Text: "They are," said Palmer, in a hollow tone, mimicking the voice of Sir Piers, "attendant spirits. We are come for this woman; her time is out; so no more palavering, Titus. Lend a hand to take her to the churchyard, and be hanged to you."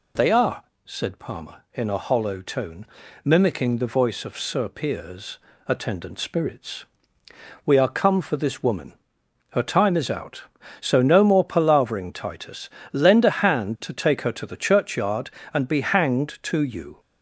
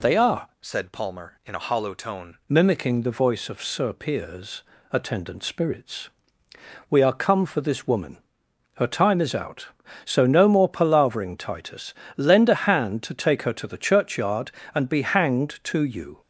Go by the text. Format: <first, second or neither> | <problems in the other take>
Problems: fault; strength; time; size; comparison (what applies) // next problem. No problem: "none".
first | changes voice from "said" to "tone"; from 0.6 to 2.3 s; 1.7 s long